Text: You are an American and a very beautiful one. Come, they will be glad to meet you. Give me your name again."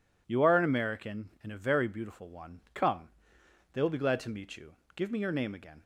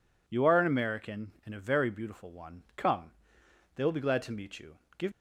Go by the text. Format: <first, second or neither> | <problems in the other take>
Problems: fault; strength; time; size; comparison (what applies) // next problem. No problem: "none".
first | stops before "me your name again"; at 5.1 s